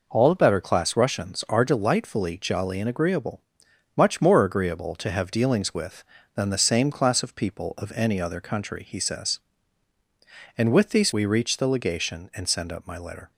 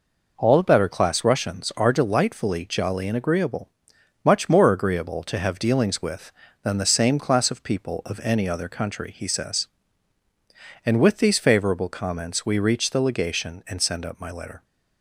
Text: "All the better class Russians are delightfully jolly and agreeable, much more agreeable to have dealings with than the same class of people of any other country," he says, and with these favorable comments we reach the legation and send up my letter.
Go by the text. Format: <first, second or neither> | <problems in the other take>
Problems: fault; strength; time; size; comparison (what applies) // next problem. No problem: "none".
second | skips "favorable comments"; at 11.1 s